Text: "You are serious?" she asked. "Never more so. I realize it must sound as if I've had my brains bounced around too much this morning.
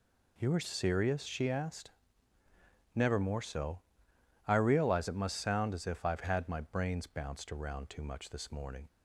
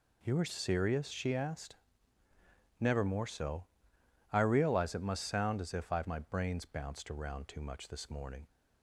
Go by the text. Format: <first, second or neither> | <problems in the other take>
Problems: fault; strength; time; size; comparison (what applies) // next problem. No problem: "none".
first | skips "had"; at 6.0 s